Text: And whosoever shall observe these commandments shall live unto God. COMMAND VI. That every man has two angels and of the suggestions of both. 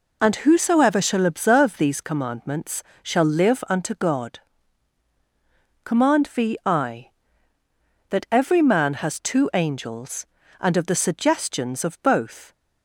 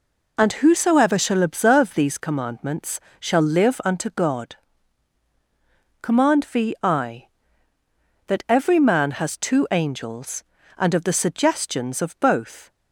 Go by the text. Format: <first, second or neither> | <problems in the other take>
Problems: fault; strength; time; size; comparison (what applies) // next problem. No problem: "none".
neither | pauses between "commandments" and "shall"; slight; the same in both